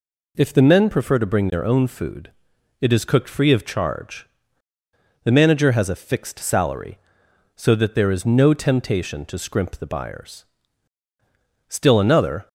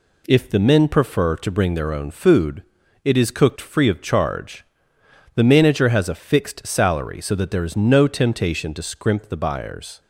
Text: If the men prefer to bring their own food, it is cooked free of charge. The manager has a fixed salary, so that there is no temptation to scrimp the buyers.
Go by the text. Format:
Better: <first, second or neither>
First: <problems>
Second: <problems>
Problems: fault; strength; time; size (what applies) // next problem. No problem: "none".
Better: second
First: goes on to say "Still another"; noticeable; from 11.6 s on; 0.80 s long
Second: none